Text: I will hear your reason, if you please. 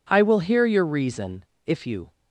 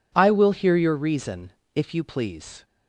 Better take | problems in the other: second | stops before "please"; at 2.1 s

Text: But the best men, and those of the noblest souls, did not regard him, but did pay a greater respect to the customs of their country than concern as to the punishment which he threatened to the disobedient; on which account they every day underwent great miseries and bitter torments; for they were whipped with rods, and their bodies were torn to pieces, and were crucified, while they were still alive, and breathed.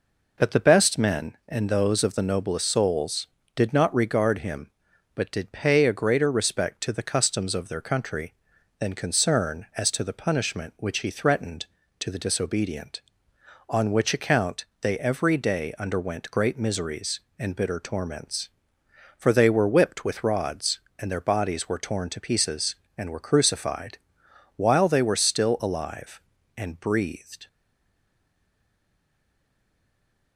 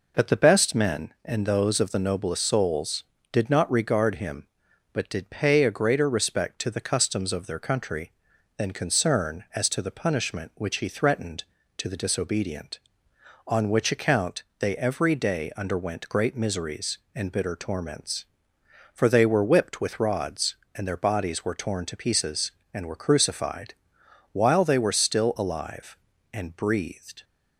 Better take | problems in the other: second | pauses between "account" and "they"; slight; at 14.6 s; 0.16 s long; slight in the second // stays silent after the last word; strong; from 27.4 s on; 2.9 s long

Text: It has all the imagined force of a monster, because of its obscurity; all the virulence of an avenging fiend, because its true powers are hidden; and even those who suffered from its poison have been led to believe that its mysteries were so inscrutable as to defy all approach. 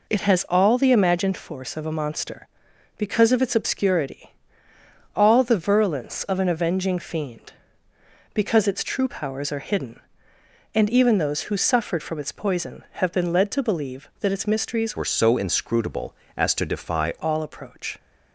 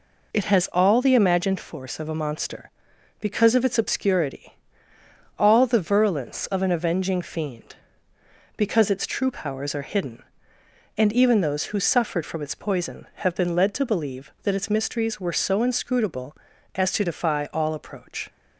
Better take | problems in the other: second | changes voice from "were" to "defy"; from 14.9 to 17.1 s; 2.2 s long

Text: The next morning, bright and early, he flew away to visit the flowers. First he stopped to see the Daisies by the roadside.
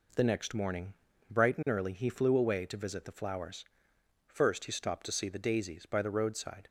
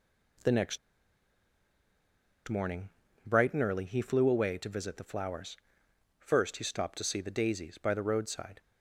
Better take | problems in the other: first | pauses between "next" and "morning"; strong; at 0.7 s; 1.7 s long

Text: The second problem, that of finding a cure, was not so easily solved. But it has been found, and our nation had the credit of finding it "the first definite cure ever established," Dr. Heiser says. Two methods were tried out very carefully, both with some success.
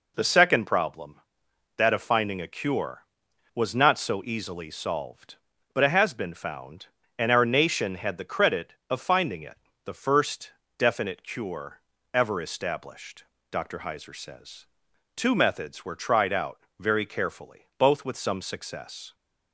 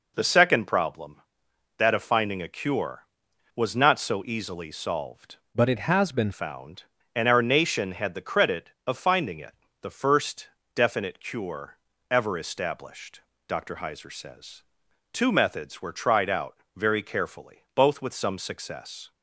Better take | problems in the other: first | changes voice from "But" to "been"; from 5.5 to 6.3 s; 0.8 s long // pauses between "it" and "the"; slight; at 9.5 s; 0.28 s long; slight in the first // pauses between "first" and "definite"; slight; at 10.4 s; 0.26 s long; slight in the first // pauses between "cure" and "ever"; slight; at 11.7 s; 0.32 s long; slight in the first // pauses between "out" and "very"; slight; at 16.5 s; 0.18 s long; slight in the first

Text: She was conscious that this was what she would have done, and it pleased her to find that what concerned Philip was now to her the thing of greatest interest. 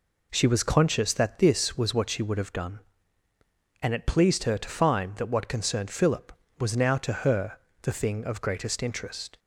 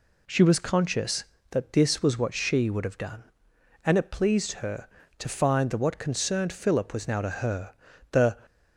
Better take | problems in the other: first | pauses between "her" and "the"; slight; at 7.7 s; 0.34 s long; slight in the first // stops before "thing of greatest interest"; at 8.4 s

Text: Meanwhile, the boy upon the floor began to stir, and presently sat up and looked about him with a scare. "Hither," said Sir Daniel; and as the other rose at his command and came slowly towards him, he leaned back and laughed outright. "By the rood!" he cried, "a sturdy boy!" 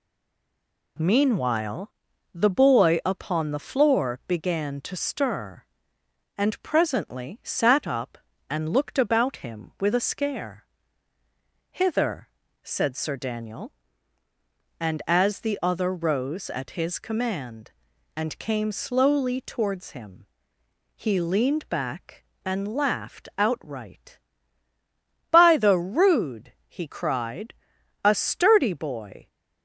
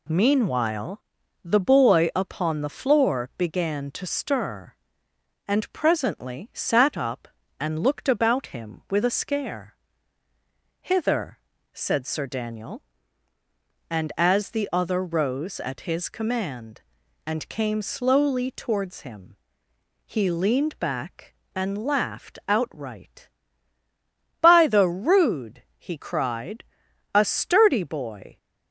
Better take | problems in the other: second | stays silent before the first word; slight; until 0.9 s; 0.9 s long

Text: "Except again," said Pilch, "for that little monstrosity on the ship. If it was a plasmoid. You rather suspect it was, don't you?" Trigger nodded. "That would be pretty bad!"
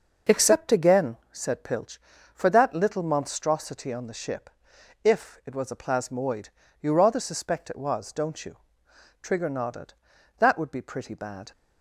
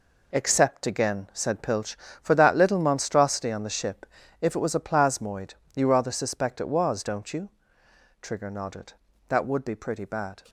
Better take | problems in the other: first | gets quieter; strong; throughout; 9 dB

